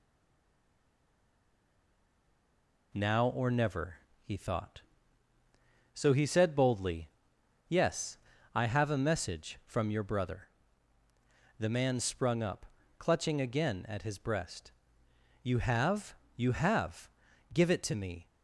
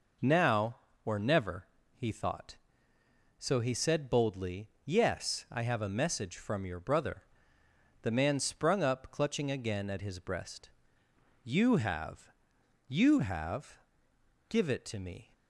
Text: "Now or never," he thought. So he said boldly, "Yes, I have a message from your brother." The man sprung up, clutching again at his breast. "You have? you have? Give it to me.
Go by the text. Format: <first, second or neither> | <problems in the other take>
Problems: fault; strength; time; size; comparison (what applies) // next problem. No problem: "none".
second | stays silent before the first word; strong; until 2.9 s; 2.9 s long